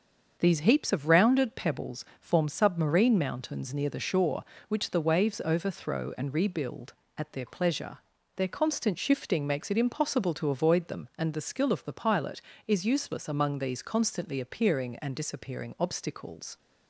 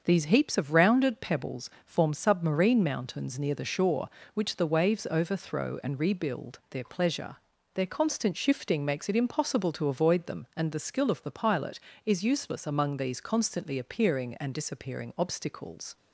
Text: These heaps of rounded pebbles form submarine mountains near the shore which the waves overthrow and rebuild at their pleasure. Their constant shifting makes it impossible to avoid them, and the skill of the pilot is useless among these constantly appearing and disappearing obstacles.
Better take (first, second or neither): first